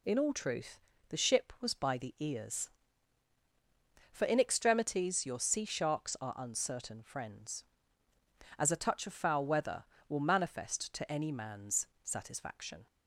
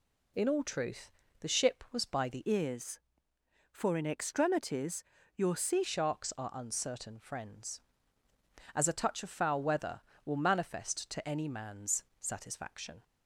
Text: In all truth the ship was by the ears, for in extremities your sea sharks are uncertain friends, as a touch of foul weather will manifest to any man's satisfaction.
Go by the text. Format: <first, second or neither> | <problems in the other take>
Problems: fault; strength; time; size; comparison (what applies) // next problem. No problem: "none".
first | pauses between "truth" and "the"; slight; at 1.1 s; 0.28 s long; slight in the first // changes voice from "ears" to "sea"; from 2.4 to 5.8 s; 3.4 s long // pauses between "extremities" and "your"; slight; at 5.0 s; 0.32 s long // pauses between "man's" and "satisfaction"; slight; at 12.0 s; 0.16 s long; slight in the first